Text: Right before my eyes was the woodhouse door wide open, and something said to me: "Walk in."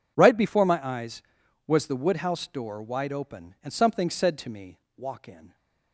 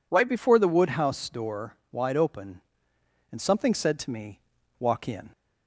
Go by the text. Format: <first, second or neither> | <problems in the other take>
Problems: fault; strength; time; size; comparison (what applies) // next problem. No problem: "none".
first | skips "my eyes was"; at 0.5 s // pauses between "door" and "wide"; slight; at 1.7 s; 0.18 s long